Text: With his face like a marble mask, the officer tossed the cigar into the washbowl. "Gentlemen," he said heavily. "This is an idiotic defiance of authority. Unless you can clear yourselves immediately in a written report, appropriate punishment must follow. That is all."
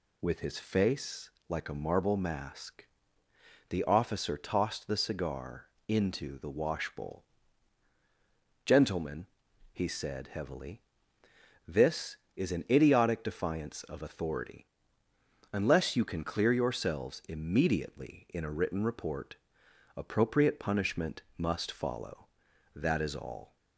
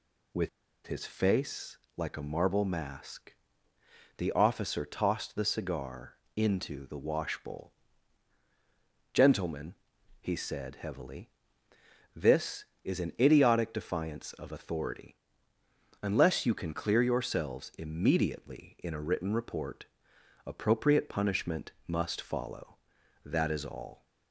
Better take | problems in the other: first | pauses between "With" and "his"; at 0.4 s; 0.37 s long // pauses between "face" and "like"; slight; at 1.7 s; 0.20 s long; slight in the first // pauses between "cigar" and "into"; slight; at 6.1 s; 0.22 s long; slight in the first

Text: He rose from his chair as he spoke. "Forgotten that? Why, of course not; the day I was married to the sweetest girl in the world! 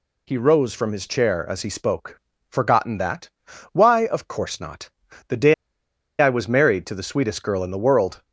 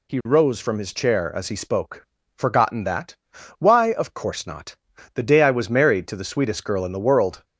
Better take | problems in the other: second | pauses between "day" and "I"; noticeable; at 5.5 s; 0.65 s long

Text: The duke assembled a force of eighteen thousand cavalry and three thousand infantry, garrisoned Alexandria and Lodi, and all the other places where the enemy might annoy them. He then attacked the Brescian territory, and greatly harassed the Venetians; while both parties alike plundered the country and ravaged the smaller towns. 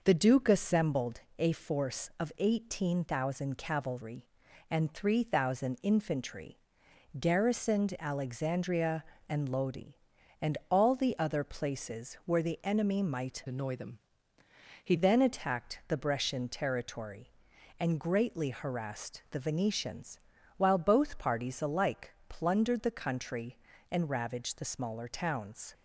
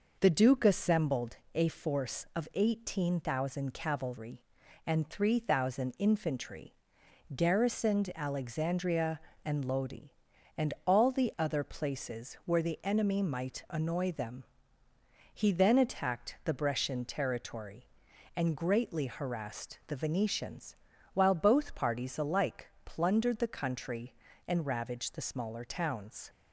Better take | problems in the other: second | pauses between "assembled" and "a"; slight; at 1.1 s; 0.18 s long; slight in the second // changes voice from "annoy" to "He"; from 13.4 to 14.9 s; 1.5 s long // pauses between "alike" and "plundered"; slight; at 22.1 s; 0.16 s long; slight in the second

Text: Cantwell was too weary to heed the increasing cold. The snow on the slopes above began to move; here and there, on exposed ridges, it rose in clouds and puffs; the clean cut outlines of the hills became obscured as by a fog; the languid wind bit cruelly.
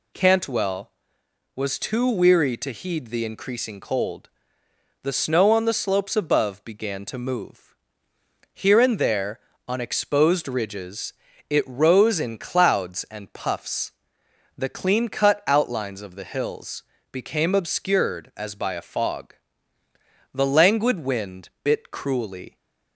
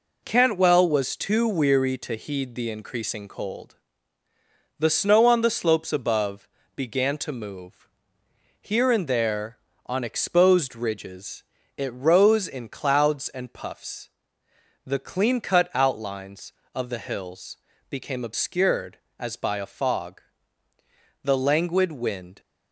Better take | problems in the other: first | pauses between "above" and "began"; slight; at 6.4 s; 0.26 s long // pauses between "hills" and "became"; slight; at 17.5 s; 0.32 s long; slight in the first // stops before "bit cruelly"; at 22.3 s

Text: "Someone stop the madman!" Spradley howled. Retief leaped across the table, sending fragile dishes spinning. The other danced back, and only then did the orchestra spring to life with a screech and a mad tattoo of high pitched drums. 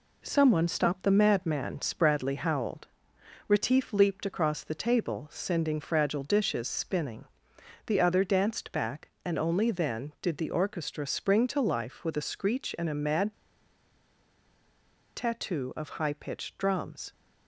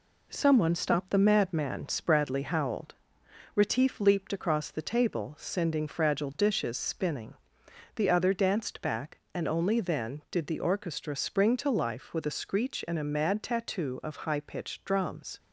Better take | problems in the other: second | pauses between "mad" and "tattoo"; strong; at 13.3 s; 1.8 s long

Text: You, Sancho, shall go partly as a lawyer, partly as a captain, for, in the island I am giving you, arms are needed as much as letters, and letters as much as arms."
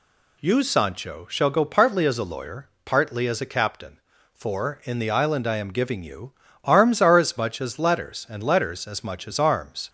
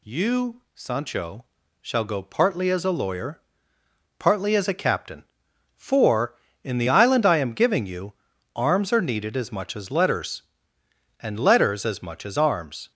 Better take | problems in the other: second | skips "needed"; at 7.1 s

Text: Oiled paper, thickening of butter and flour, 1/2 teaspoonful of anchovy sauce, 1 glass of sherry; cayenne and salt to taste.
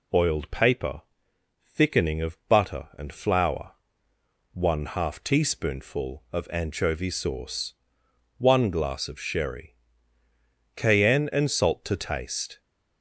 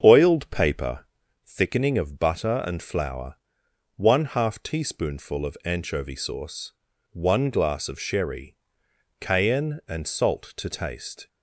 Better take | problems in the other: first | starts louder than the rest; until 1.5 s; 7 dB

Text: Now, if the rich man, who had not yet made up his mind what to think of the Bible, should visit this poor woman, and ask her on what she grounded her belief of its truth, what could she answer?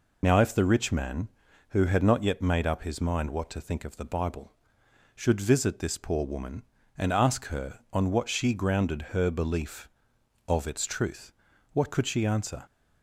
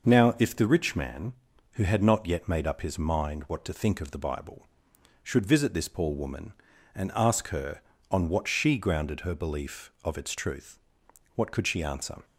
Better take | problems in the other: second | loses the start of "Now"; at 0.2 s; 45 ms

